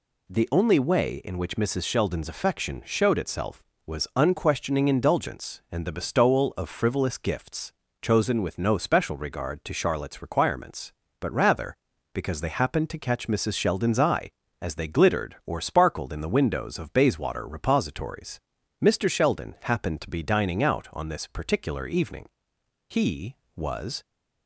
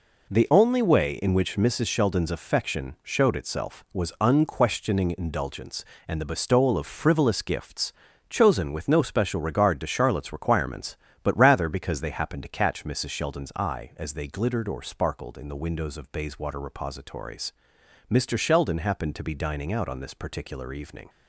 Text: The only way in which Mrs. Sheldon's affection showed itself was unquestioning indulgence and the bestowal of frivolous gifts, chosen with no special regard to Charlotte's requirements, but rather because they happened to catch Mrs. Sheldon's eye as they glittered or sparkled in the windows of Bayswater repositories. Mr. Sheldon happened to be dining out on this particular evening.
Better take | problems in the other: second | goes on to say "He was"; noticeable; from 22.8 s on; 1.1 s long

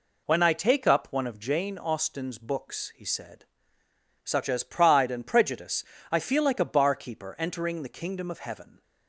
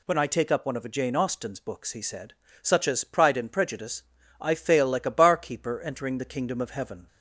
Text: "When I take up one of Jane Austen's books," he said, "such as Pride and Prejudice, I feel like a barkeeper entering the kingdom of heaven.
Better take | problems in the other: first | says "fail" for "feel"; at 4.5 s

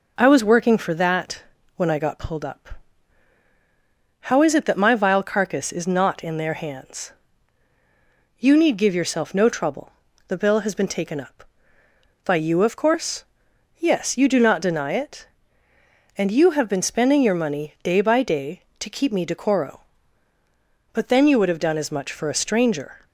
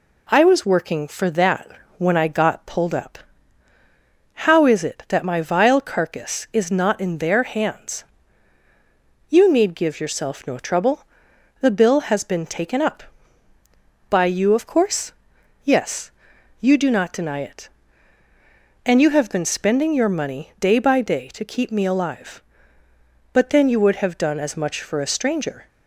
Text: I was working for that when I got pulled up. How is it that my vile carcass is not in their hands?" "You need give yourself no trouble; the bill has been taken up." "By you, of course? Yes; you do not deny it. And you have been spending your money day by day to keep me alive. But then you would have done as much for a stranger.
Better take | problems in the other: second | pauses between "that" and "when"; slight; at 1.4 s; 0.32 s long; slight in the second // says "decoro" for "alive"; at 19.2 s

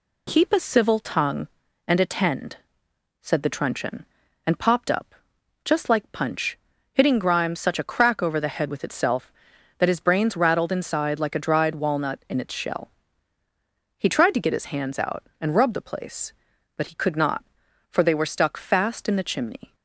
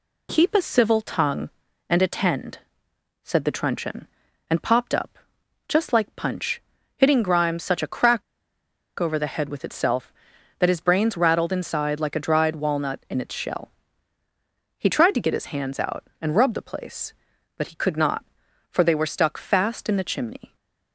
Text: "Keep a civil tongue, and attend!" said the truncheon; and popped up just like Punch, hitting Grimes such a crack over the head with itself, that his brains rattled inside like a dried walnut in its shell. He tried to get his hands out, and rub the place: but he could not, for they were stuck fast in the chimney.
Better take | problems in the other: first | pauses between "up" and "just"; noticeable; at 5.1 s; 0.50 s long; noticeable in the first // pauses between "crack" and "over"; noticeable; at 8.2 s; 0.77 s long

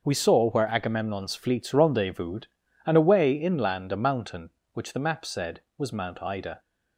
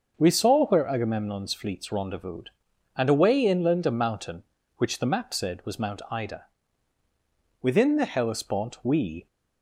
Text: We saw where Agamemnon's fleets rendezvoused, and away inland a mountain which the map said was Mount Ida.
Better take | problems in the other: first | starts louder than the rest; noticeable; until 1.1 s; 6 dB; also in the first // goes on to say "Within the Hellespont we"; from 7.6 s on; 1.6 s long

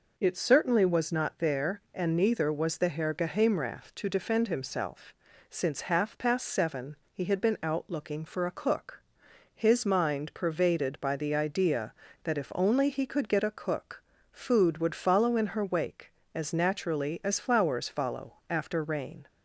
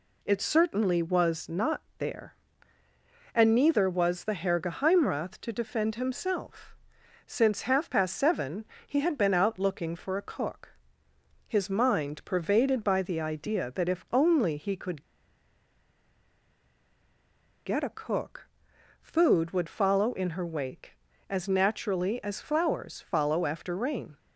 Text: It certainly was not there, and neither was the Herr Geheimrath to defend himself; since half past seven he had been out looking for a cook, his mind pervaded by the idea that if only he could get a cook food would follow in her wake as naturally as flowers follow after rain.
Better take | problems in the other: first | pauses between "not" and "there"; slight; at 1.8 s; 0.16 s long // pauses between "seven" and "he"; slight; at 8.6 s; 0.22 s long; slight in the first // pauses between "could" and "get"; strong; at 15.0 s; 2.6 s long // pauses between "cook" and "food"; noticeable; at 18.4 s; 0.52 s long; slight in the first

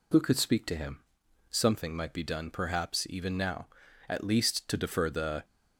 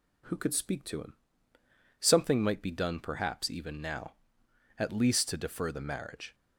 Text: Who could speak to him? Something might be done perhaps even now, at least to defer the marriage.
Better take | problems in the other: second | stops before "marriage"; at 5.4 s

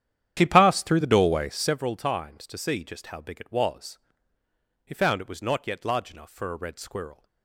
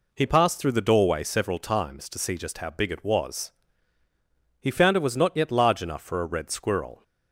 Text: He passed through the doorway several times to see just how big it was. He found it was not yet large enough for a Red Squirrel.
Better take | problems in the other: second | starts louder than the rest; strong; until 1.8 s; 10 dB

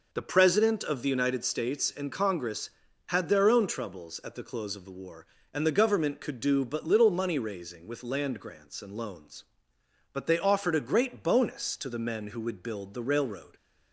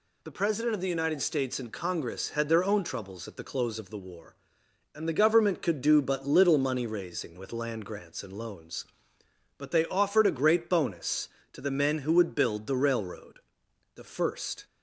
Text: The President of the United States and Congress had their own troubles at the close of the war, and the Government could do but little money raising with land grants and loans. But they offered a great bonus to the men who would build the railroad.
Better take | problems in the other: first | goes on to say "The first"; noticeable; from 13.9 s on; 0.70 s long

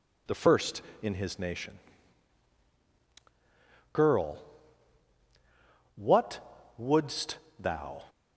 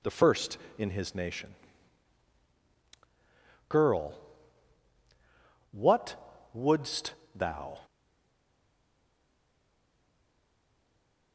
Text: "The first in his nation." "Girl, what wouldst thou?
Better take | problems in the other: first | pauses between "what" and "wouldst"; at 6.1 s; 0.38 s long; also in the first // pauses between "wouldst" and "thou"; slight; at 7.1 s; 0.20 s long; slight in the first // stays silent after the last word; strong; from 7.8 s on; 3.5 s long

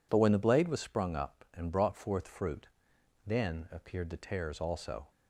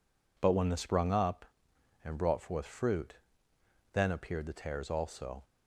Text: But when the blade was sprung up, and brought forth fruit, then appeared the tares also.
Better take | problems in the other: first | skips "blade was"; at 0.7 s

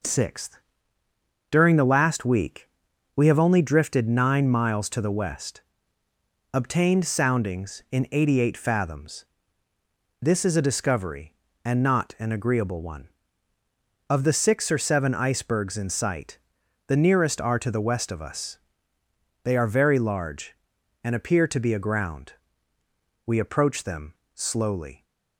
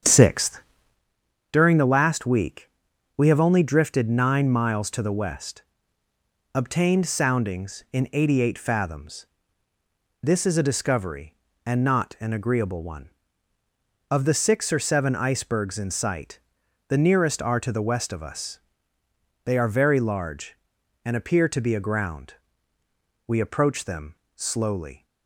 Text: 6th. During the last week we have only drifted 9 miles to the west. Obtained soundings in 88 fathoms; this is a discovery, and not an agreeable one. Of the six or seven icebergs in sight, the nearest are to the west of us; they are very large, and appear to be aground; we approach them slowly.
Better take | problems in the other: first | starts louder than the rest; strong; until 1.0 s; 8 dB // pauses between "week" and "we"; noticeable; at 2.6 s; 0.48 s long; noticeable in the first // pauses between "them" and "slowly"; slight; at 24.1 s; 0.20 s long; slight in the first

